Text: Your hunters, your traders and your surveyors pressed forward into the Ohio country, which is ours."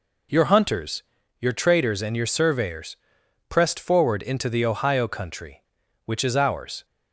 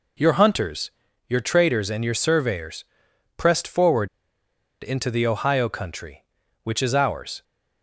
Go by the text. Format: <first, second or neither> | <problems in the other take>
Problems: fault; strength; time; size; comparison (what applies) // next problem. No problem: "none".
first | pauses between "surveyors" and "pressed"; noticeable; at 2.8 s; 0.54 s long; noticeable in the first // pauses between "forward" and "into"; noticeable; at 4.0 s; 0.74 s long